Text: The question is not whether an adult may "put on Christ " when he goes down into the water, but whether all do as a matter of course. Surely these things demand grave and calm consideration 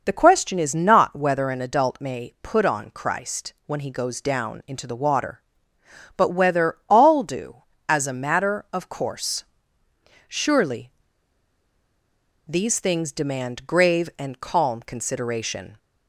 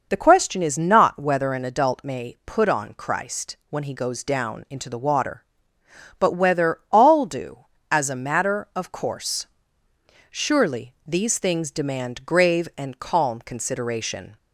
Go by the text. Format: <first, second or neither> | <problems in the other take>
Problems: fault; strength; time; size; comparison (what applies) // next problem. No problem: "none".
second | pauses between "Surely" and "these"; strong; at 10.8 s; 1.5 s long